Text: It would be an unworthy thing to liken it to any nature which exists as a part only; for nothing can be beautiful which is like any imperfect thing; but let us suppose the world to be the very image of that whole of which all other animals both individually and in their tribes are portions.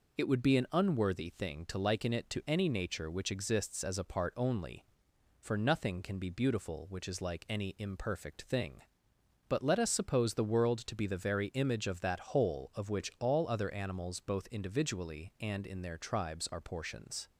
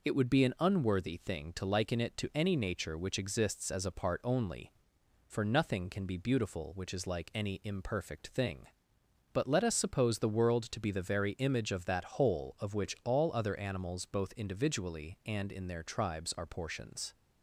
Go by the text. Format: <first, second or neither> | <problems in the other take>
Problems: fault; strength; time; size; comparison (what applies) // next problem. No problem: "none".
neither | none